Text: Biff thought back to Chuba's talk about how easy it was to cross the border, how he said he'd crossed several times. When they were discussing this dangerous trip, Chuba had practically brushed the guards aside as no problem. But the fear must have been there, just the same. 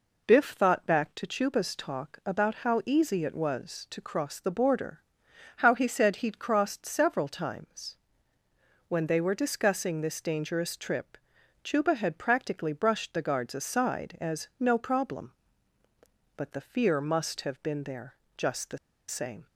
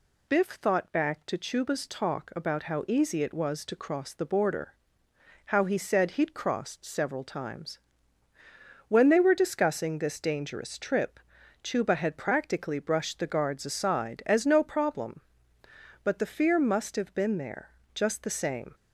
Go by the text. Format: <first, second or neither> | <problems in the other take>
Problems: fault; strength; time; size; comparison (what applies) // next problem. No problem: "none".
second | pauses between "the" and "same"; slight; at 18.7 s; 0.31 s long